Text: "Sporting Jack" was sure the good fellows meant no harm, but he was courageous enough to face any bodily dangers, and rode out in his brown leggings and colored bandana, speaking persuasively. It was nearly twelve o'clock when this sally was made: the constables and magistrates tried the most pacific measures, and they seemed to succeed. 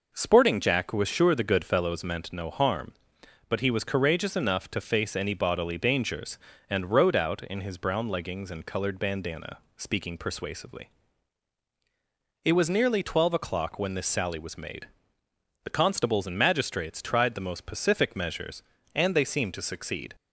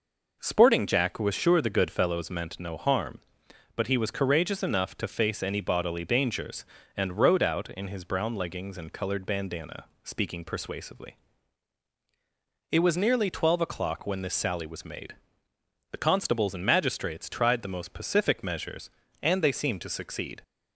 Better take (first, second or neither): neither